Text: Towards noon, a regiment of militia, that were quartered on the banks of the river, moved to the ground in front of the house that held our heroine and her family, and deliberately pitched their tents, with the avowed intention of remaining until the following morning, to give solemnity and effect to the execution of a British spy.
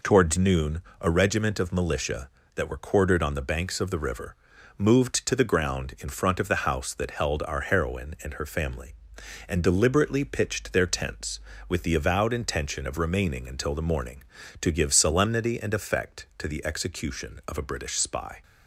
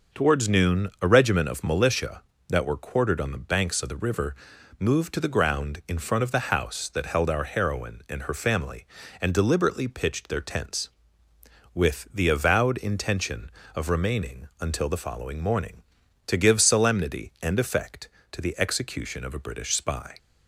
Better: second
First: skips "following"; at 13.8 s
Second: none

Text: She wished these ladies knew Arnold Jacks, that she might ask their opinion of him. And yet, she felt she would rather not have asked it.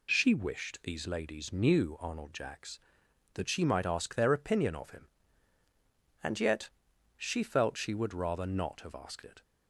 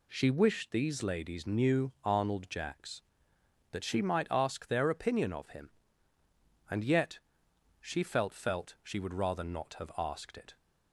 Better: first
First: none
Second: says "felt" twice; at 8.3 s

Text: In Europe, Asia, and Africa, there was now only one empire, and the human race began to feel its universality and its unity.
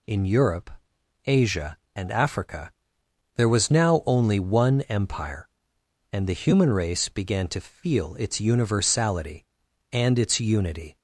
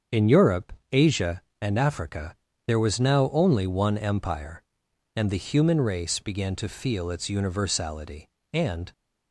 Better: first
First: none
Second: starts louder than the rest; strong; until 1.3 s; 7 dB // stops before "its unity"; at 8.9 s

